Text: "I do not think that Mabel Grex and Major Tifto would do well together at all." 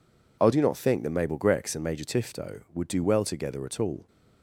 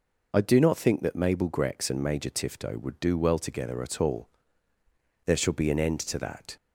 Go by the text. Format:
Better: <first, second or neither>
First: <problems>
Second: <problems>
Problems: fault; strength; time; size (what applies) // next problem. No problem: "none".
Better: first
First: none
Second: goes on to say "There shall be an end to that"; from 5.2 s on; 1.3 s long